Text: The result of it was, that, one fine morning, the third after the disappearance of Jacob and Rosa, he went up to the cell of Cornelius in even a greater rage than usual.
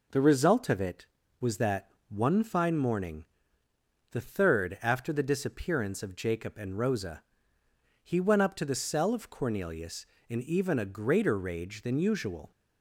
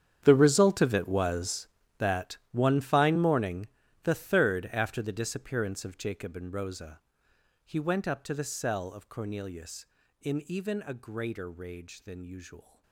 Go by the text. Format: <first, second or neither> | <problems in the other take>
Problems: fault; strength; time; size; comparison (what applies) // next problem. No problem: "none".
first | gets quieter; strong; throughout; 18.5 dB